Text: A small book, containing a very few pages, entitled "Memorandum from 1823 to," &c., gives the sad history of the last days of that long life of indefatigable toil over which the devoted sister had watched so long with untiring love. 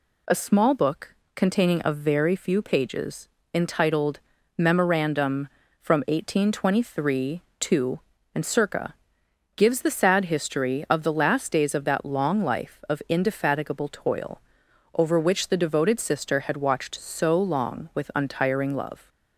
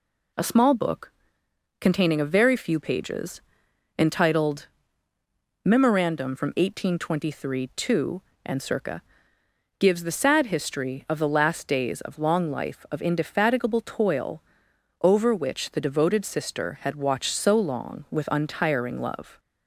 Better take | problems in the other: first | pauses between "entitled" and "Memorandum"; noticeable; at 4.6 s; 0.96 s long; slight in the first // skips "that"; at 12.1 s // pauses between "toil" and "over"; noticeable; at 14.4 s; 0.62 s long; noticeable in the first

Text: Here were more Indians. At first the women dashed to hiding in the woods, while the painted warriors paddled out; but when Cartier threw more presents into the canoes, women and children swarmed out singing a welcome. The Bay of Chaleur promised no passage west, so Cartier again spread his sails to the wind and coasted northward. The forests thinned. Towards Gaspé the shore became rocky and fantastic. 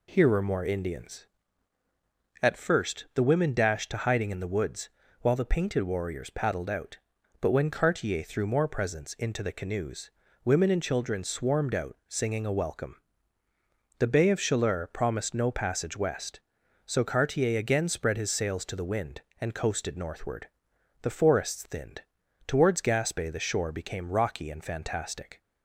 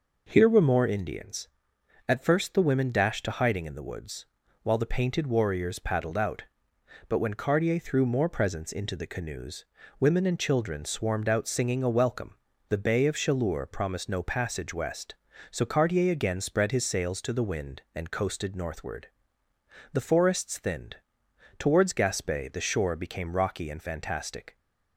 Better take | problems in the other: neither | none

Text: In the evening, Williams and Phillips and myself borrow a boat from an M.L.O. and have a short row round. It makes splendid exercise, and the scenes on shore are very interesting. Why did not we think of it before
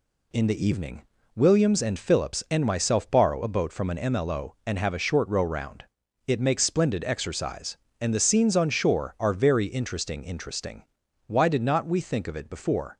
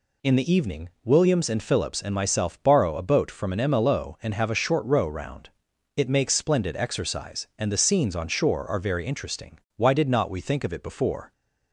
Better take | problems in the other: second | says "interesting" twice; at 10.2 s

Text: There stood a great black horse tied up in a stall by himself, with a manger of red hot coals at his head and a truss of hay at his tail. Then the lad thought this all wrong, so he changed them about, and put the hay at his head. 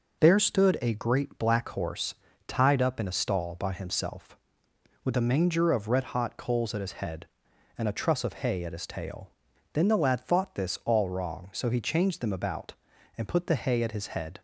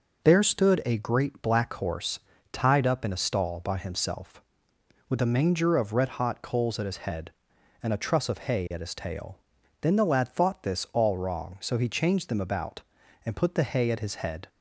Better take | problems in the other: neither | pauses between "horse" and "tied"; slight; the same in both

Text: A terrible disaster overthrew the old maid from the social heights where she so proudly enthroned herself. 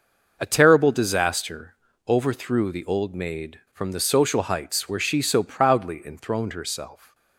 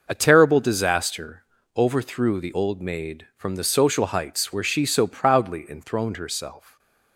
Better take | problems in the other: neither | pauses between "disaster" and "overthrew"; slight; the same in both

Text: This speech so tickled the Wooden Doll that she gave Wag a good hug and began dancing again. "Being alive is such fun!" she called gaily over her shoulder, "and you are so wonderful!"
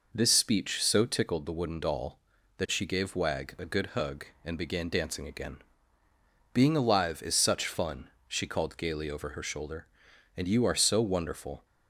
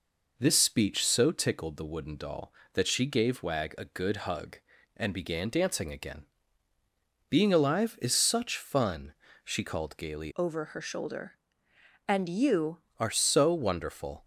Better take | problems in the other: first | changes voice from "over" to "you"; from 10.3 to 12.7 s; 2.4 s long

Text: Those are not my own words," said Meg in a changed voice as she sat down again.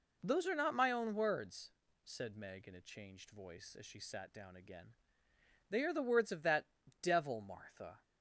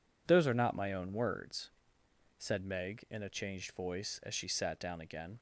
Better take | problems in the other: second | goes on to say "They are the words of that devil Martha"; strong; from 5.6 s on; 2.3 s long

